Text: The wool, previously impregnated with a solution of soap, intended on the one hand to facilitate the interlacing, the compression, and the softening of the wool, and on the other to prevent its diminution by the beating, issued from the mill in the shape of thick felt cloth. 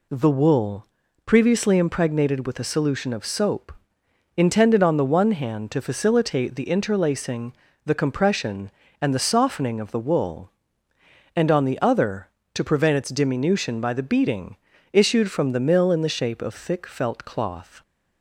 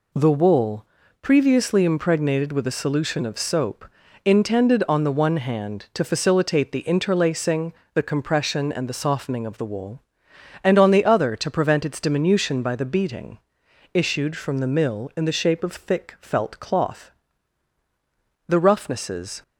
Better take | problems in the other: first | goes on to say "The roughnesses"; noticeable; from 18.4 s on; 0.96 s long

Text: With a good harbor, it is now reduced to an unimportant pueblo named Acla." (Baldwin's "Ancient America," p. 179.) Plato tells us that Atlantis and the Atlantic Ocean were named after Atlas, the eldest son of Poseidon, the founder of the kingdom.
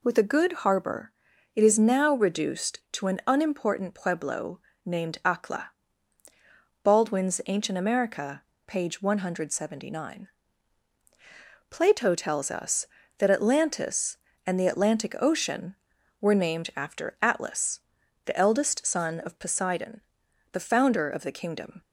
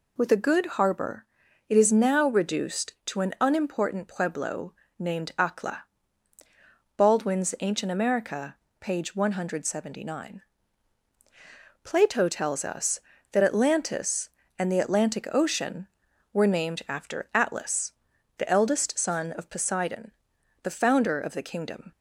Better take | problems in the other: neither | pauses between "pueblo" and "named"; slight; the same in both

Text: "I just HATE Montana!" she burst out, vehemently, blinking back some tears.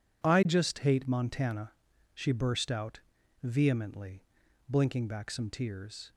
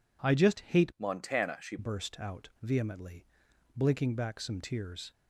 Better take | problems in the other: first | changes voice from "Montana" to "she"; from 0.9 to 1.7 s; 0.8 s long

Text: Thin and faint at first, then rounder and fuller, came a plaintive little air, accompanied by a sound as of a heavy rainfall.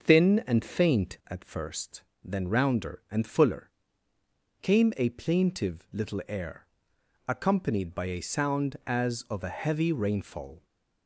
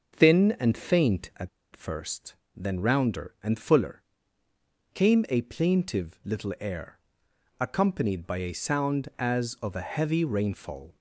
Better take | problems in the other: first | starts louder than the rest; until 1.2 s; 6.5 dB; also in the first // pauses between "at" and "first"; slight; at 1.4 s; 0.25 s long

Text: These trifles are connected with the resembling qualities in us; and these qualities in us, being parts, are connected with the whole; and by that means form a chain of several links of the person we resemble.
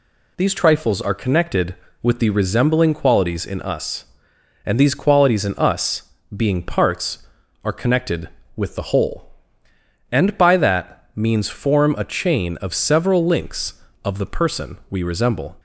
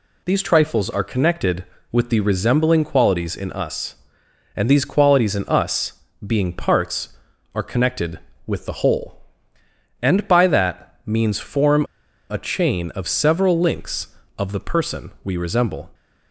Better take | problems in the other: first | pauses between "form" and "a"; noticeable; at 11.8 s; 0.46 s long

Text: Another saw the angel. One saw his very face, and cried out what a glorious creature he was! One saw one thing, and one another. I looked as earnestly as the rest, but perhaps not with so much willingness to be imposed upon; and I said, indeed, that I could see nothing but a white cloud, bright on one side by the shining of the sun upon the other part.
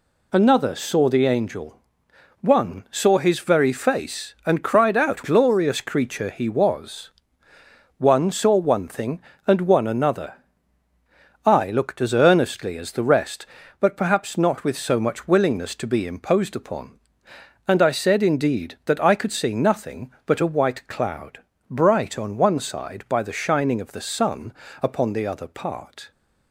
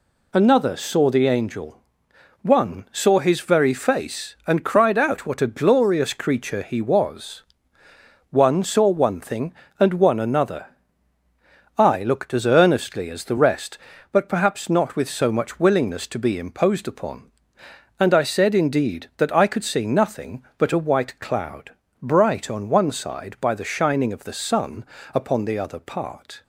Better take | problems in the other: second | skips "what a"; at 5.2 s // pauses between "sun" and "upon"; slight; at 24.5 s; 0.28 s long; slight in the second

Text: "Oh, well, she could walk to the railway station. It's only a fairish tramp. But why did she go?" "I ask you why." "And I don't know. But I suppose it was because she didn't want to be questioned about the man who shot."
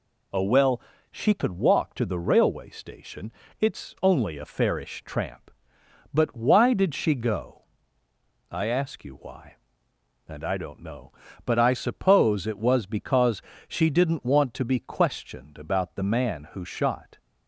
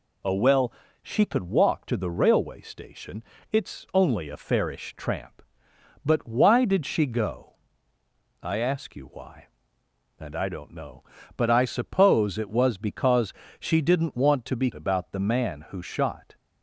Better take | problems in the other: first | pauses between "because" and "she"; slight; at 13.3 s; 0.28 s long; slight in the first // skips "questioned"; at 14.7 s

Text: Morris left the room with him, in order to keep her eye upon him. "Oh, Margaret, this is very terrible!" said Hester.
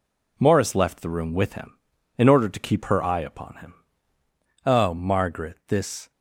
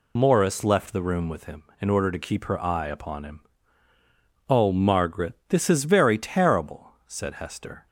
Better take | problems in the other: second | stops before "is very terrible said Hester"; at 6.1 s

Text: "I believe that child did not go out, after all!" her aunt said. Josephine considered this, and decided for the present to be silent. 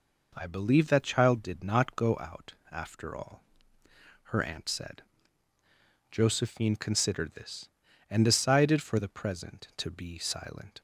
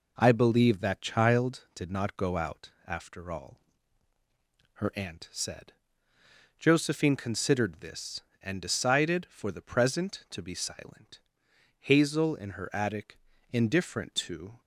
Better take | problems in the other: first | goes on to say "Hazel in her attic indifferent to"; strong; from 11.8 s on; 2.8 s long

